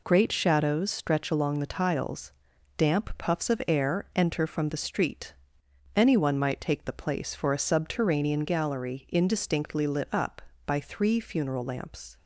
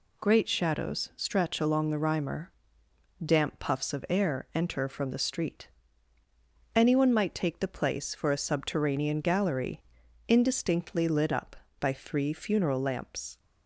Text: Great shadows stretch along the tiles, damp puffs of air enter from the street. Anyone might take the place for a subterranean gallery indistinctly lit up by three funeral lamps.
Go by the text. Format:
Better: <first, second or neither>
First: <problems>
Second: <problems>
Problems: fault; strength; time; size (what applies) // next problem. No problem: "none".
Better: first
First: none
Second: says "rhymer" for "tiles"; at 1.9 s // pauses between "gallery" and "indistinctly"; at 9.8 s; 0.45 s long